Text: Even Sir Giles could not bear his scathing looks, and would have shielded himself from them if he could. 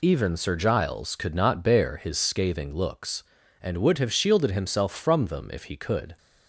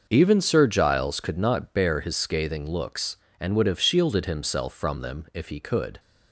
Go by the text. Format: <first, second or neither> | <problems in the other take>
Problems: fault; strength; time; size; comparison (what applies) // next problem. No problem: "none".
first | starts louder than the rest; noticeable; until 1.3 s; 6 dB